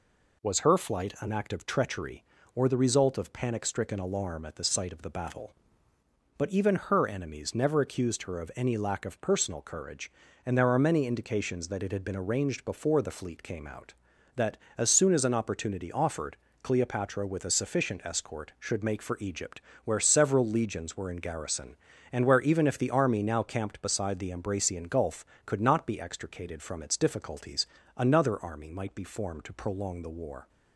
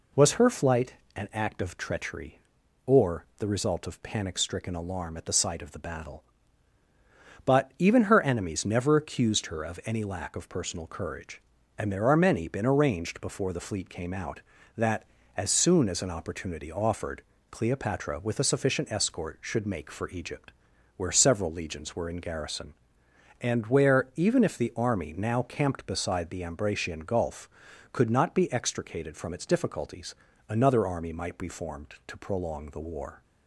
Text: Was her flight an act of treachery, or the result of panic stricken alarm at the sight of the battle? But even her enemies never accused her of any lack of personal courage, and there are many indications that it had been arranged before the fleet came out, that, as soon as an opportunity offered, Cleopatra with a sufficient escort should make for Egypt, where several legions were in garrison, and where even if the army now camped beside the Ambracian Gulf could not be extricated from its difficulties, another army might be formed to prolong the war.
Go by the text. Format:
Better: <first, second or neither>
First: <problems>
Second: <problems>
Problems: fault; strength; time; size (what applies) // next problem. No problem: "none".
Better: first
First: none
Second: pauses between "flight" and "an"; slight; at 0.9 s; 0.24 s long // skips "indications that it had"; at 12.4 s